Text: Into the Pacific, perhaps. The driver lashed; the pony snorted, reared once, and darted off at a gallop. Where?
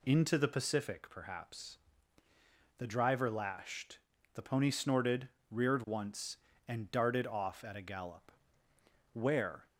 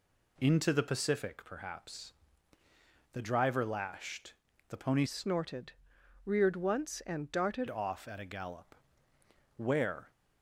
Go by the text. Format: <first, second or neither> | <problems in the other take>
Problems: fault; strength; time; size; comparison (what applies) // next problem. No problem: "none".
first | changes voice from "snorted" to "darted"; from 5.0 to 7.6 s; 2.6 s long